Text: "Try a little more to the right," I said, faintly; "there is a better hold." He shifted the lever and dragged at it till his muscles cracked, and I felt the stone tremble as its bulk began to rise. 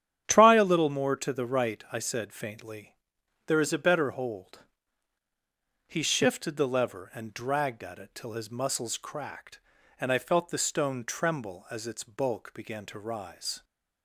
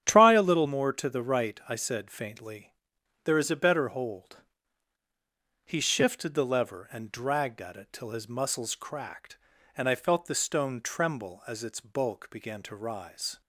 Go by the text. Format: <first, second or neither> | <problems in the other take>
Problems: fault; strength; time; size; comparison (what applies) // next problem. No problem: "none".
neither | starts louder than the rest; strong; the same in both